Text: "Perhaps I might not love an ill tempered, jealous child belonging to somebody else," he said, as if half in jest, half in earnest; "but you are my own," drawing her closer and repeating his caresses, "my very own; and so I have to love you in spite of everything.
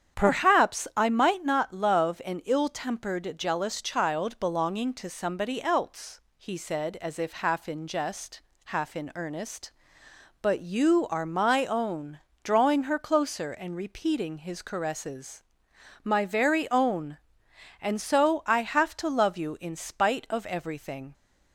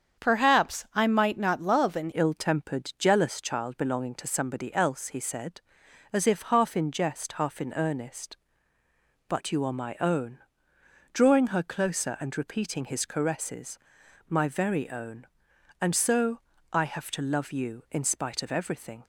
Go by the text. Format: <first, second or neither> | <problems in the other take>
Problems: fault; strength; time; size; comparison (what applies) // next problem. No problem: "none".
first | starts louder than the rest; strong; until 1.2 s; 7.5 dB; strong in the first // changes voice at "ill"; from 2.1 s on; 16.9 s long // pauses between "so" and "I"; slight; at 16.4 s; 0.32 s long